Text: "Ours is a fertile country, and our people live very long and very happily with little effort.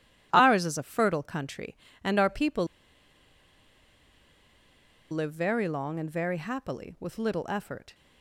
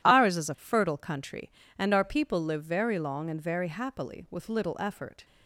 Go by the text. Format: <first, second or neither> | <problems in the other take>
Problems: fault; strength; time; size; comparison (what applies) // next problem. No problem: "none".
second | pauses between "people" and "live"; strong; at 2.6 s; 2.4 s long